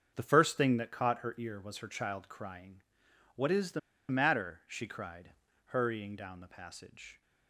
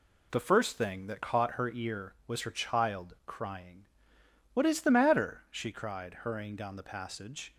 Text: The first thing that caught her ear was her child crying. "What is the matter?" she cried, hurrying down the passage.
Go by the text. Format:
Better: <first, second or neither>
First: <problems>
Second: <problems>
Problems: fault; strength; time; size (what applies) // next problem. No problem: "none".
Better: second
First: starts louder than the rest; until 1.1 s; 7 dB // pauses between "the" and "matter"; slight; at 3.7 s; 0.31 s long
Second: none